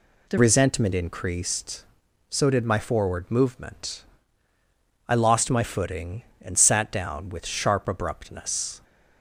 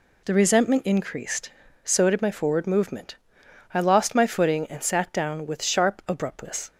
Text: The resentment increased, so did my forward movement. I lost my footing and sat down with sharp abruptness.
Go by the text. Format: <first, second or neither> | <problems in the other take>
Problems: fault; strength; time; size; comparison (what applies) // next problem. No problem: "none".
second | changes voice at "resentment"; from 0.3 s on; 8.5 s long